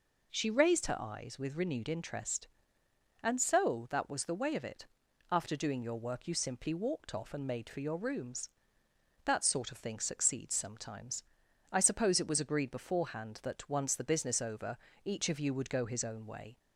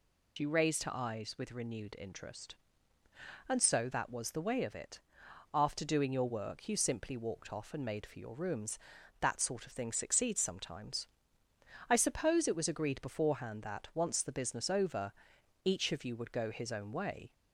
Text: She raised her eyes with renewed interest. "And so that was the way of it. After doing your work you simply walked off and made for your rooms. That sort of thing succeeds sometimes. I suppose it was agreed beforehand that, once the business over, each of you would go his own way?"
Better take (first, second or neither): first